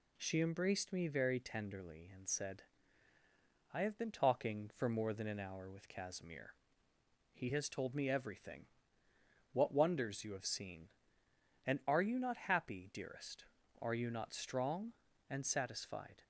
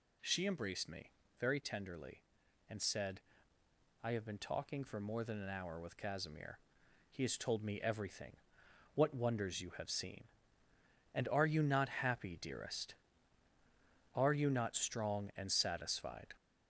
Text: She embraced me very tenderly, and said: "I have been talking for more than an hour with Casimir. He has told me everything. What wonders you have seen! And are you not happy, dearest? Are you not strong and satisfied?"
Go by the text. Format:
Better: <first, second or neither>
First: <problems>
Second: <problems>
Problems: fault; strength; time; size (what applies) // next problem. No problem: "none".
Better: first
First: none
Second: gets louder; noticeable; throughout; 4 dB // pauses between "me" and "very"; slight; at 1.1 s; 0.28 s long